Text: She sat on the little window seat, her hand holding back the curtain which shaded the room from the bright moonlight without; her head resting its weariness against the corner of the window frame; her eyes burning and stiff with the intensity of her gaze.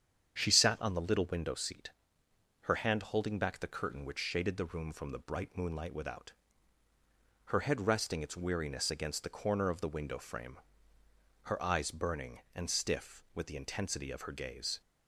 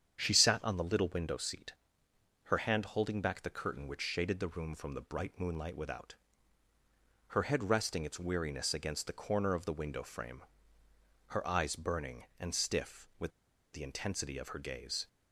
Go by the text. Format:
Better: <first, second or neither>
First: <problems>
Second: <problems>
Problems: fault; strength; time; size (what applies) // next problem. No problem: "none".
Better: first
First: starts louder than the rest; strong; until 1.4 s; 8.5 dB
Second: starts louder than the rest; strong; until 1.2 s; 8.5 dB // pauses between "with" and "the"; at 13.3 s; 0.42 s long